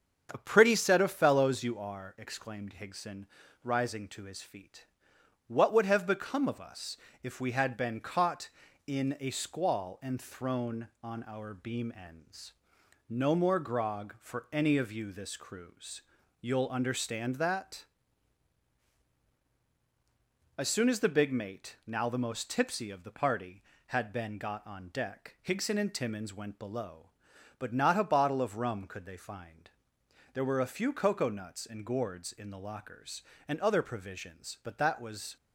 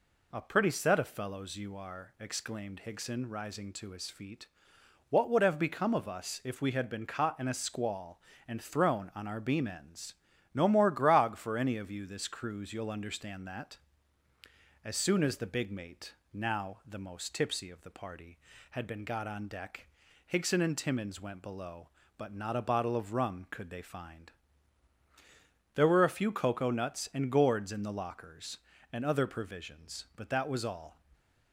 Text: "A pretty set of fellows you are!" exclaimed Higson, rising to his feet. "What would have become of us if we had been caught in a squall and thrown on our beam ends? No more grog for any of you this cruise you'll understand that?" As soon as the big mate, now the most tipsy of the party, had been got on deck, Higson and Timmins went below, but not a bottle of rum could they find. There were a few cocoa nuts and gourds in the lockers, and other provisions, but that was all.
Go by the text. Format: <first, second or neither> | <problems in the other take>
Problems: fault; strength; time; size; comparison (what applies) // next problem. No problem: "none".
second | starts louder than the rest; strong; until 1.3 s; 7 dB // pauses between "us" and "if"; slight; at 6.9 s; 0.26 s long // pauses between "cruise" and "you'll"; at 16.0 s; 0.38 s long // stops before "all"; at 35.3 s